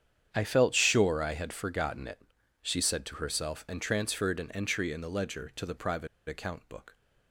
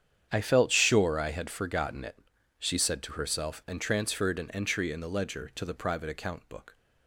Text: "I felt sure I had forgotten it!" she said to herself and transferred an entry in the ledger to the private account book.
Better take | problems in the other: second | starts louder than the rest; strong; until 1.3 s; 8.5 dB; strong in the second // pauses between "private" and "account"; slight; at 6.0 s; 0.21 s long

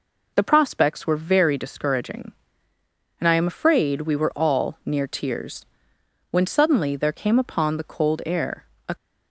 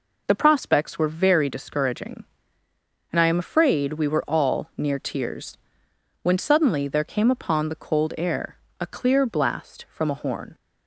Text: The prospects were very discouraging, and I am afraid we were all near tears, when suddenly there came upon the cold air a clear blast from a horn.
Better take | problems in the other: second | pauses between "air" and "a"; slight; at 8.6 s; 0.24 s long; slight in the second // stops before "clear blast from a horn"; at 8.9 s

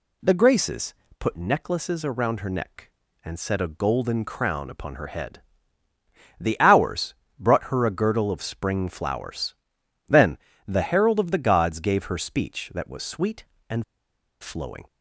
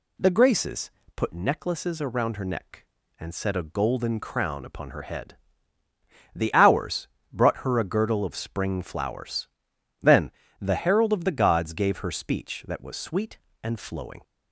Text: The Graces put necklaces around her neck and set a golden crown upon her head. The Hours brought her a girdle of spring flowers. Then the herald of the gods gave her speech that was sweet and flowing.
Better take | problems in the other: second | pauses between "Graces" and "put"; slight; at 0.9 s; 0.24 s long; slight in the second // pauses between "Hours" and "brought"; slight; at 7.1 s; 0.26 s long; slight in the second // pauses between "Then" and "the"; slight; at 10.3 s; 0.30 s long; slight in the second // pauses between "and" and "flowing"; noticeable; at 13.8 s; 0.57 s long

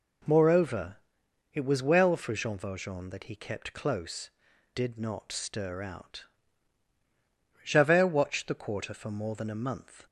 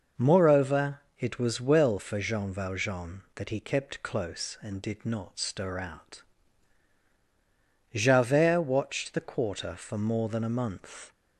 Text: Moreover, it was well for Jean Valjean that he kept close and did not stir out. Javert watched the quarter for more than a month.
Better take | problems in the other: second | skips "and"; at 4.5 s

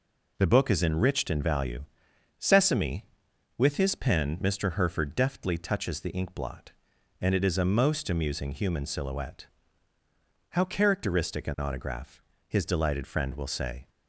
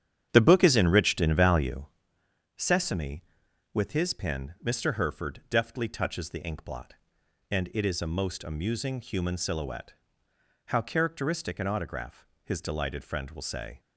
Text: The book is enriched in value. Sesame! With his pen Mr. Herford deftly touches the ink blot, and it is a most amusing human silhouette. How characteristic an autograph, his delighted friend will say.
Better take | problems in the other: first | starts louder than the rest; strong; until 2.1 s; 9.5 dB

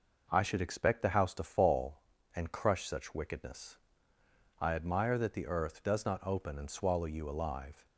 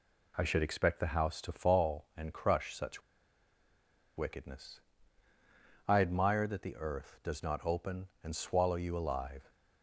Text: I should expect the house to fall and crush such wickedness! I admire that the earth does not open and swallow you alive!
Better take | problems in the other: first | pauses between "such" and "wickedness"; at 3.0 s; 1.1 s long

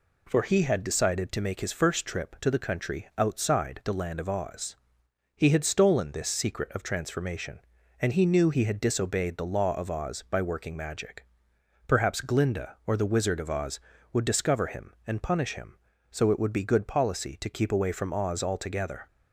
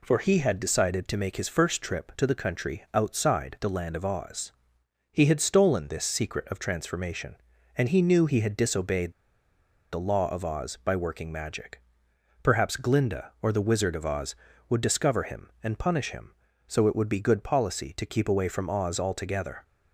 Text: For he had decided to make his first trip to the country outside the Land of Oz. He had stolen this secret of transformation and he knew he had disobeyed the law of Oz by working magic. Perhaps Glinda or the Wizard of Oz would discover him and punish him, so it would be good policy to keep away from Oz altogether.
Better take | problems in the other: first | pauses between "disobeyed" and "the"; noticeable; at 9.1 s; 0.78 s long

